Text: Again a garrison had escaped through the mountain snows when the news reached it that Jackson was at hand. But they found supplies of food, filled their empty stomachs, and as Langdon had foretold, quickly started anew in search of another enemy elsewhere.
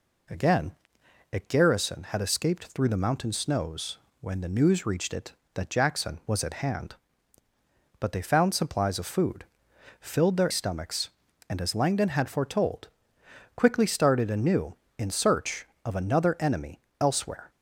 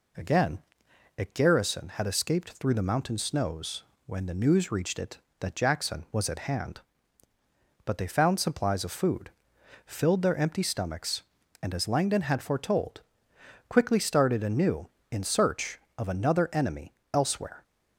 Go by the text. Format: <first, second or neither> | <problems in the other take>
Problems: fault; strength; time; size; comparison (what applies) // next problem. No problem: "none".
second | pauses between "Again" and "a"; noticeable; at 0.7 s; 0.62 s long; noticeable in the second // pauses between "snows" and "when"; slight; at 3.9 s; 0.24 s long; slight in the second // skips "empty"; at 10.5 s // pauses between "enemy" and "elsewhere"; slight; at 16.7 s; 0.20 s long; slight in the second